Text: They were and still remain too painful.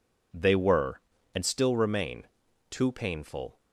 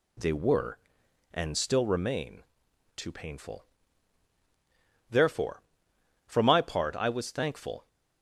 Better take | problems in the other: first | pauses between "remain" and "too"; noticeable; at 2.4 s; 0.54 s long; also in the first // goes on to say "Therefore for my part I was thankful"; strong; from 5.1 s on; 2.7 s long

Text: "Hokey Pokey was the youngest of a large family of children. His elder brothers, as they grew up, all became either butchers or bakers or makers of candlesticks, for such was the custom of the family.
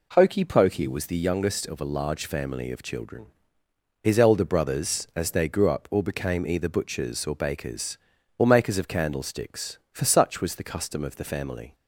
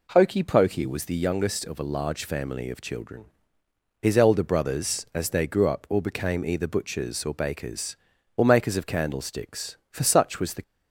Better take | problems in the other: first | stops before "custom of the family"; at 10.6 s

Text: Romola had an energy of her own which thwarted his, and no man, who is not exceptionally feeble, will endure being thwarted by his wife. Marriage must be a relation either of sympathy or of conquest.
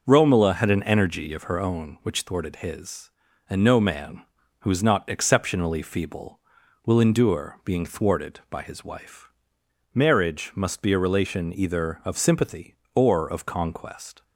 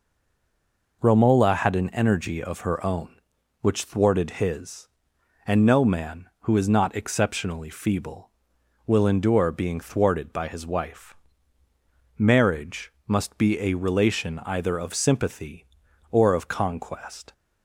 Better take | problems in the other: first | stays silent before the first word; until 1.0 s; 1.0 s long

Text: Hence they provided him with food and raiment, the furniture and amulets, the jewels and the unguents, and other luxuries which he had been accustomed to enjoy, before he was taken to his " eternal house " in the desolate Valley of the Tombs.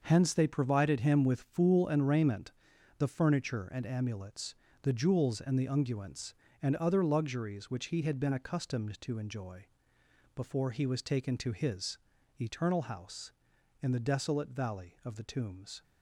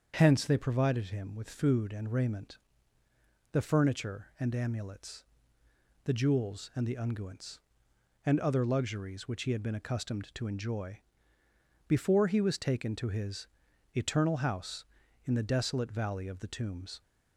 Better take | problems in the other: second | starts louder than the rest; until 1.0 s; 6 dB; also in the second // says "fool" for "food"; at 1.4 s

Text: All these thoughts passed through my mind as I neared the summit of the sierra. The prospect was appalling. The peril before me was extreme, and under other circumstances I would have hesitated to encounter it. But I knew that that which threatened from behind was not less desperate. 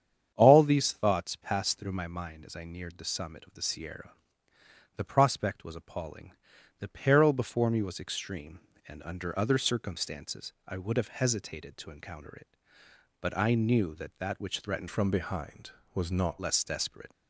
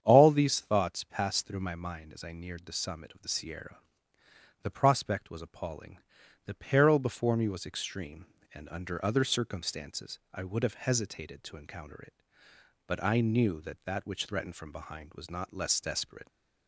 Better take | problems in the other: second | starts louder than the rest; strong; until 1.3 s; 8.5 dB; strong in the second // changes voice from "from" to "not"; from 14.8 to 16.4 s; 1.6 s long

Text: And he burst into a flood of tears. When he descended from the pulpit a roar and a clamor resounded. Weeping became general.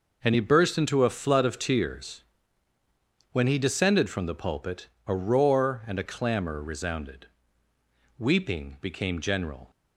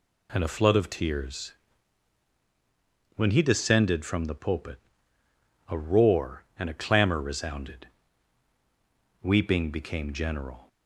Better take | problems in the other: first | skips "he burst into"; at 0.4 s // pauses between "pulpit" and "a"; noticeable; at 4.7 s; 0.90 s long; slight in the first

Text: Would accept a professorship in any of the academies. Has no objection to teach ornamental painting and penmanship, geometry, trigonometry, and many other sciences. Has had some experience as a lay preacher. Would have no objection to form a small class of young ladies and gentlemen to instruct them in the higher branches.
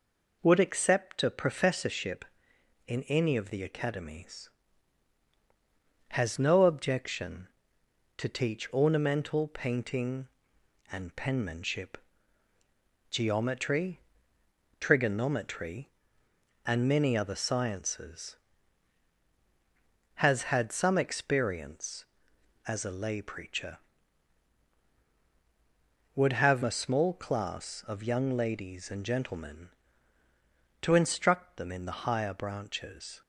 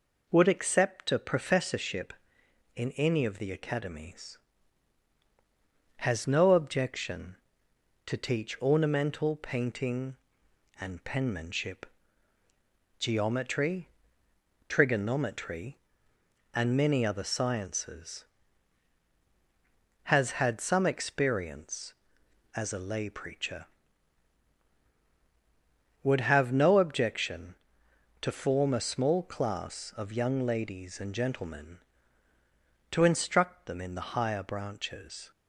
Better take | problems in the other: second | skips "no objection to form"; at 26.6 s

